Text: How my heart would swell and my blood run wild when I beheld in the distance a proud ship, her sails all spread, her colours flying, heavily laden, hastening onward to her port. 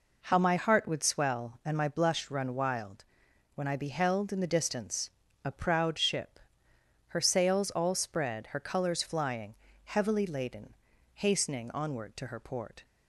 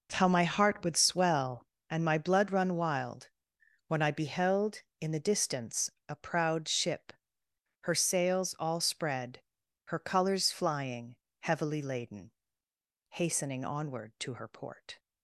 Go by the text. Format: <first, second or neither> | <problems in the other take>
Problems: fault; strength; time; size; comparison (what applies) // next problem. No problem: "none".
second | says "blush" for "blood"; at 1.8 s // pauses between "wild" and "when"; noticeable; at 3.0 s; 0.50 s long; noticeable in the second // pauses between "distance" and "a"; slight; at 5.0 s; 0.34 s long; slight in the second